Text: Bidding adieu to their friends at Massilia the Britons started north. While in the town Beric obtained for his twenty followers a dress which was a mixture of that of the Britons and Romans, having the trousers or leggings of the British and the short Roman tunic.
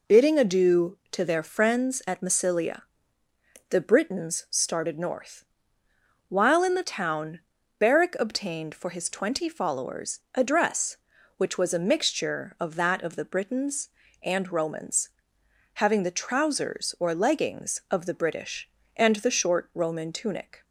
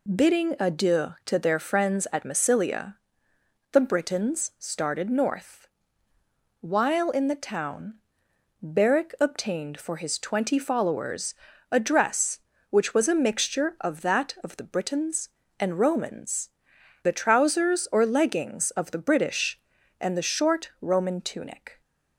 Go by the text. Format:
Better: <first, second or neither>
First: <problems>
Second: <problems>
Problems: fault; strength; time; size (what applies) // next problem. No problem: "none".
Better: first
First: pauses between "Massilia" and "the"; noticeable; at 2.8 s; 0.88 s long // pauses between "town" and "Beric"; at 7.3 s; 0.40 s long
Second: pauses between "Massilia" and "the"; noticeable; at 2.9 s; 0.78 s long // pauses between "town" and "Beric"; noticeable; at 7.9 s; 0.68 s long // pauses between "followers" and "a"; at 11.3 s; 0.38 s long // skips "having"; at 16.7 s